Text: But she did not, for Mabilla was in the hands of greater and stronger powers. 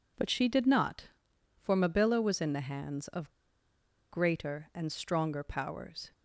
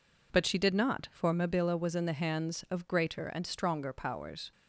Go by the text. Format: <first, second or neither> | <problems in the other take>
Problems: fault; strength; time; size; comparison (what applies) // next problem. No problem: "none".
second | pauses between "of" and "greater"; noticeable; at 3.3 s; 0.79 s long